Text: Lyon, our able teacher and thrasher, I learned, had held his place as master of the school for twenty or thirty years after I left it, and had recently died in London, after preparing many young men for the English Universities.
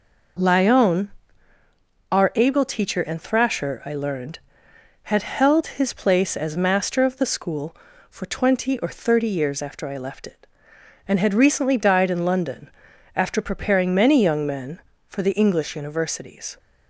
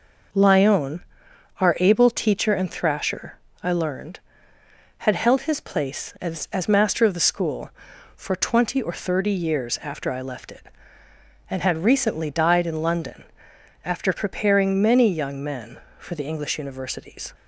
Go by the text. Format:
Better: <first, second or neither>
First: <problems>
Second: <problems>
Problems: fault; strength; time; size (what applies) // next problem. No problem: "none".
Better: first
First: none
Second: says "as" twice; at 6.5 s